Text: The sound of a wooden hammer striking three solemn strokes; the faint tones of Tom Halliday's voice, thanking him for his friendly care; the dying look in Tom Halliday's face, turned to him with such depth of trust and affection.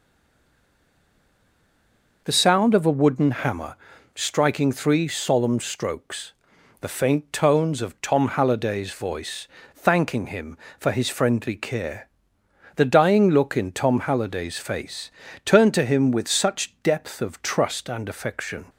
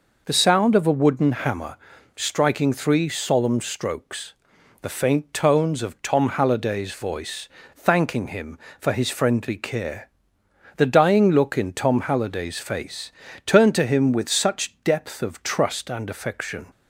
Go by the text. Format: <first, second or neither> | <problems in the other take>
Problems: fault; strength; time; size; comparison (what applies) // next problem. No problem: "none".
second | stays silent before the first word; until 2.2 s; 2.2 s long // pauses between "hammer" and "striking"; slight; at 3.7 s; 0.36 s long; slight in the second